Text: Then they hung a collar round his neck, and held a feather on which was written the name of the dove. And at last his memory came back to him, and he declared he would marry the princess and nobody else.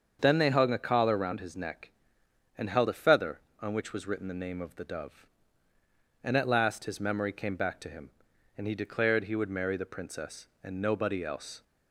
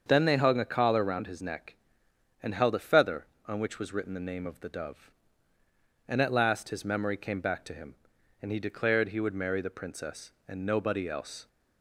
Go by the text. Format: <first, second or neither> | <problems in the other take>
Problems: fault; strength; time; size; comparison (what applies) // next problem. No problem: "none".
neither | starts louder than the rest; the same in both